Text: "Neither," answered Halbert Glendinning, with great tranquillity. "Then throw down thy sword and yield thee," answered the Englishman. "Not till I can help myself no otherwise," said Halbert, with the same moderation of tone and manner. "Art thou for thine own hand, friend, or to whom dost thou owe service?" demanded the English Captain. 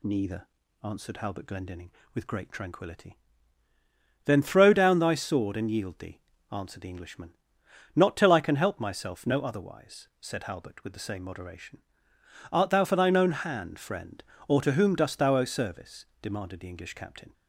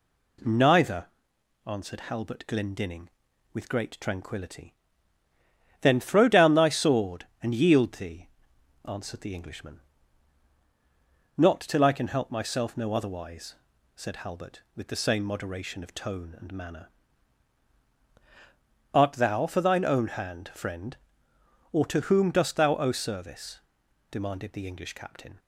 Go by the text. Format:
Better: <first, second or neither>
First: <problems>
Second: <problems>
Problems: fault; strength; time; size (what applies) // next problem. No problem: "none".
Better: second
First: skips "of tone and manner"; at 12.1 s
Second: none